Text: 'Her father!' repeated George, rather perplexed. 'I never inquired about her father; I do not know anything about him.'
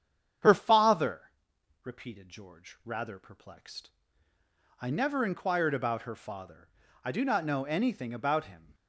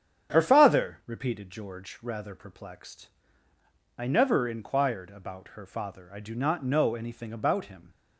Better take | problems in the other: neither | starts louder than the rest; strong; the same in both

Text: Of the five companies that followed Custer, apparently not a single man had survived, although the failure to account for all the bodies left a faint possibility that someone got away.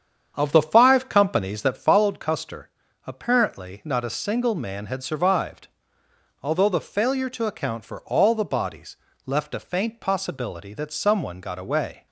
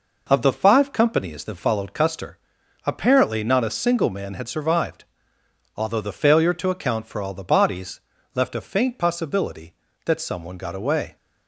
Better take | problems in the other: second | starts louder than the rest; strong; until 2.0 s; 8 dB // pauses between "bodies" and "left"; slight; at 8.9 s; 0.30 s long; slight in the second

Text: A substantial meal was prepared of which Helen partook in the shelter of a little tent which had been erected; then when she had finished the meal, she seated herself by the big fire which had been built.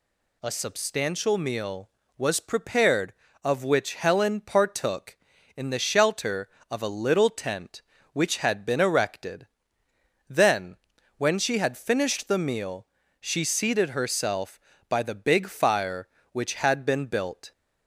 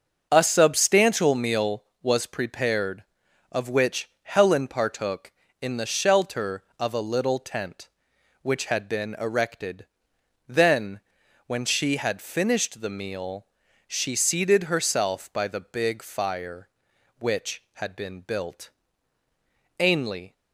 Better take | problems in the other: first | starts louder than the rest; noticeable; until 1.3 s; 6 dB // pauses between "then" and "when"; noticeable; at 10.9 s; 0.48 s long; also in the first // goes on to say "Ainley"; from 19.7 s on; 0.54 s long

